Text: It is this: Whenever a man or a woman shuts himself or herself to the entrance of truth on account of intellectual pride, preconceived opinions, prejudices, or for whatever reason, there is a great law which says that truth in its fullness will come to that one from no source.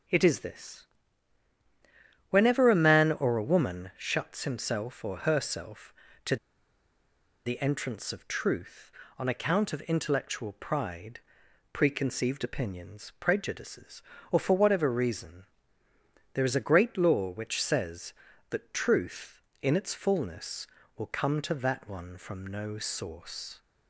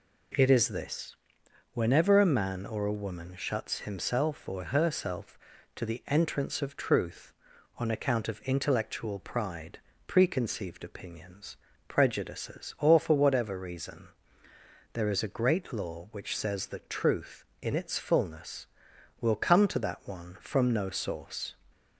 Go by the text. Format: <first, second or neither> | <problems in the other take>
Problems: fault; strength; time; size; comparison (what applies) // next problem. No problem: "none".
second | pauses between "to" and "the"; at 6.3 s; 1.0 s long